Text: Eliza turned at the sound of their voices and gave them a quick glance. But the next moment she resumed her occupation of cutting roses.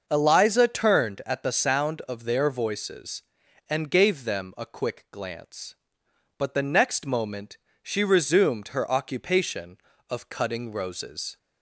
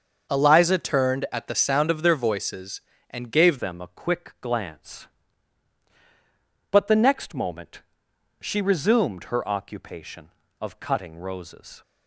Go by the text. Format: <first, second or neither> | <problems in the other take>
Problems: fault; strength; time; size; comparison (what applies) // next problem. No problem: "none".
first | starts louder than the rest; until 1.3 s; 6.5 dB; noticeable in the first // changes voice at "them"; from 3.5 s on; 8.3 s long // pauses between "moment" and "she"; noticeable; at 7.8 s; 0.58 s long; slight in the first